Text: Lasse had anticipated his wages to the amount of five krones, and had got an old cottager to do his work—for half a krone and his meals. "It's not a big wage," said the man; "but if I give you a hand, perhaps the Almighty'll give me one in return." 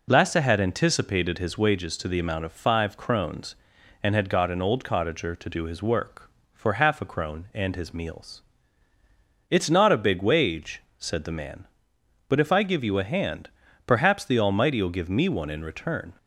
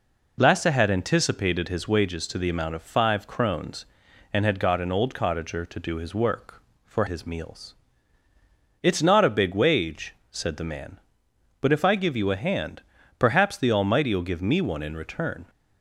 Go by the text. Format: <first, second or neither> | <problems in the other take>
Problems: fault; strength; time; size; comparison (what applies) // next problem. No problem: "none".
first | skips "half a krone and"; at 7.0 s